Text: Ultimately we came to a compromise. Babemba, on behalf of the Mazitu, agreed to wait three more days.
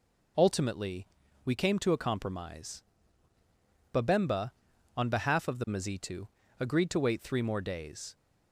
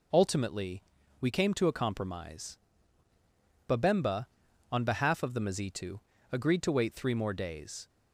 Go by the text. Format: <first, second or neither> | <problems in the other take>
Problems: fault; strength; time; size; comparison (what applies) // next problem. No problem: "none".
neither | pauses between "Ultimately" and "we"; the same in both